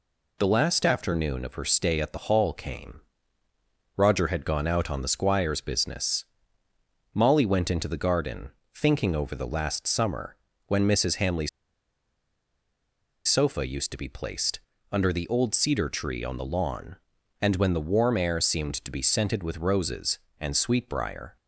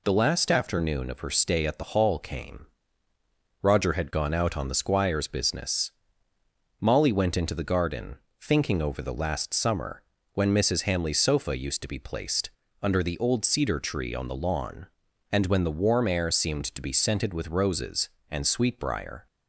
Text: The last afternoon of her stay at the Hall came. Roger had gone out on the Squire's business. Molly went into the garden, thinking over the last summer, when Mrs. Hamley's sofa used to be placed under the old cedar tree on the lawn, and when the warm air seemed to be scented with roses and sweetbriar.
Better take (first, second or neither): second